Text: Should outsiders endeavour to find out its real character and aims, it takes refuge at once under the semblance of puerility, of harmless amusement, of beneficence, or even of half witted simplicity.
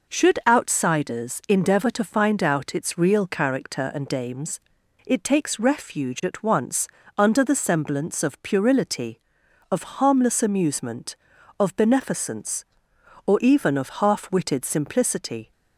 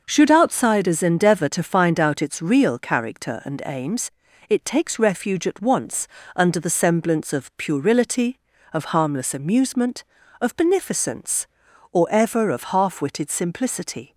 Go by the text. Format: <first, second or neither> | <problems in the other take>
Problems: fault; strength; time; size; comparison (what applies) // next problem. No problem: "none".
first | pauses between "once" and "under"; slight; at 6.0 s; 0.26 s long; slight in the first // says "ever" for "even"; at 12.1 s